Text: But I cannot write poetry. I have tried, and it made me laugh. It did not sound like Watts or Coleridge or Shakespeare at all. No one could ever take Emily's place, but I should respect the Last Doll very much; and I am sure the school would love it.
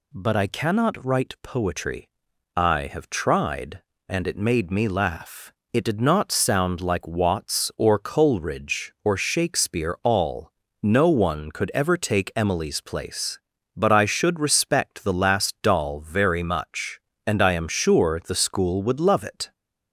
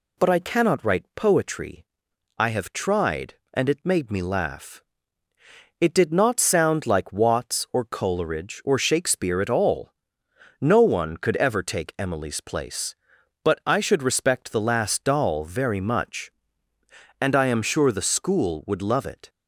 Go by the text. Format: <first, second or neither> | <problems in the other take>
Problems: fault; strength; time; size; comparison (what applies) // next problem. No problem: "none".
second | skips "at"; at 10.0 s